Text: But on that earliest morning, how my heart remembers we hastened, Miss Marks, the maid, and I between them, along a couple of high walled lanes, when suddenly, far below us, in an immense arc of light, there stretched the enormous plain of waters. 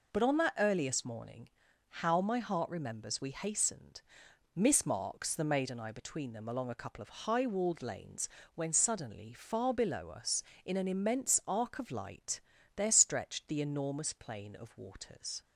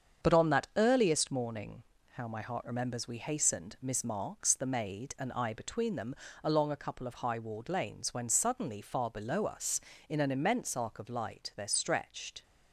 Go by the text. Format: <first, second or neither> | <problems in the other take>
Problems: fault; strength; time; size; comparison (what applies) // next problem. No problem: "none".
first | starts louder than the rest; strong; until 1.3 s; 7.5 dB // stops before "the enormous plain of waters"; at 12.4 s